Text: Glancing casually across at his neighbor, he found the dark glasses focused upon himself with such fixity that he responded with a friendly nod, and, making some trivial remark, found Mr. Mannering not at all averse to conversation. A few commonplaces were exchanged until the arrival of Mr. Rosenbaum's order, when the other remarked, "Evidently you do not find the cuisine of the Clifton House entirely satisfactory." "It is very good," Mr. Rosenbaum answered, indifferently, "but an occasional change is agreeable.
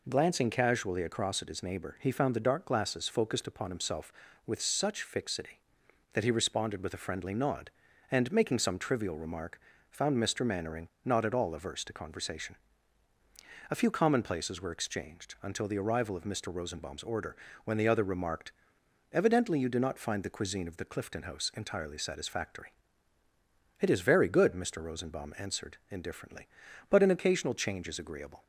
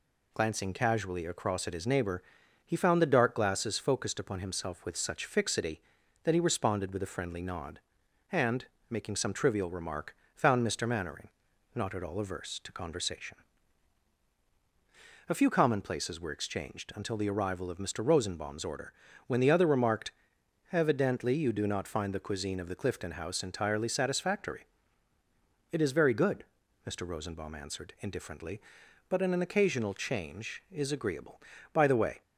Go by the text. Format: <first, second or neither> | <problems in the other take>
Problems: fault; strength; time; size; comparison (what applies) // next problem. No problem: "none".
first | pauses between "Mannering" and "not"; noticeable; at 11.2 s; 0.46 s long; slight in the first // goes on to say "By the way"; slight; from 31.7 s on; 0.48 s long